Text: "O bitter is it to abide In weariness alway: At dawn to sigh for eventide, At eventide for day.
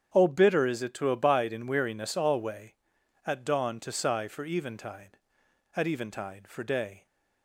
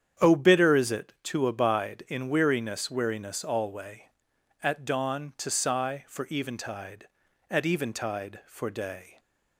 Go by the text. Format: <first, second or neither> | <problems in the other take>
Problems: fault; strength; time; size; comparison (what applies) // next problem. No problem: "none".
first | starts louder than the rest; strong; until 1.3 s; 8.5 dB; strong in the first // says "weariness" twice; at 2.8 s